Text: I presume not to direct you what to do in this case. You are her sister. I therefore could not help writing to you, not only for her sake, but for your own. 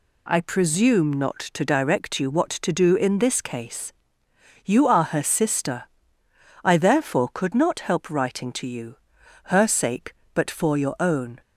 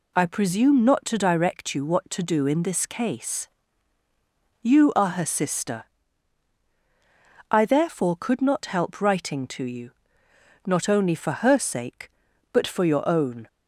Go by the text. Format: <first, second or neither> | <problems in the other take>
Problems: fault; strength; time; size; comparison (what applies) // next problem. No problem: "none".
second | skips "not only for"; at 9.2 s